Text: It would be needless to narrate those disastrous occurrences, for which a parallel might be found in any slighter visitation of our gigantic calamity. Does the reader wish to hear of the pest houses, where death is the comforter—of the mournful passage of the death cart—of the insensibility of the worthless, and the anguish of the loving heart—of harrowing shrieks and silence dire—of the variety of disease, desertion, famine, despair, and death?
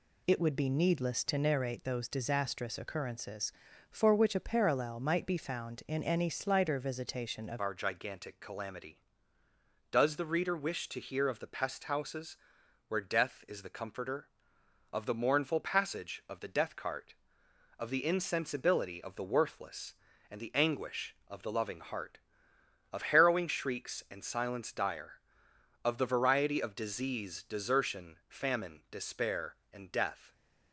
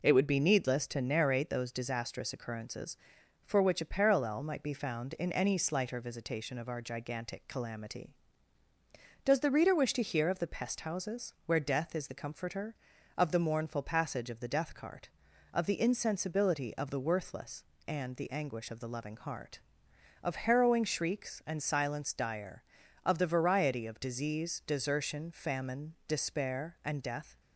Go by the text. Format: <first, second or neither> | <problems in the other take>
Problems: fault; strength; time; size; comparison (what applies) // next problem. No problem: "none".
second | changes voice at "our"; from 7.6 s on; 22.7 s long